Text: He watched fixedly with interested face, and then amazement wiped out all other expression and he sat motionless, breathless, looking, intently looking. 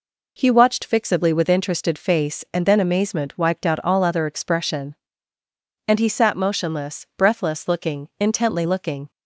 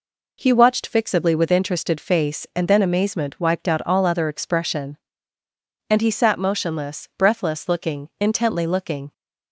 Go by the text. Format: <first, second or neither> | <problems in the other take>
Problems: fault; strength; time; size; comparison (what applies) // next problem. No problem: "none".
neither | none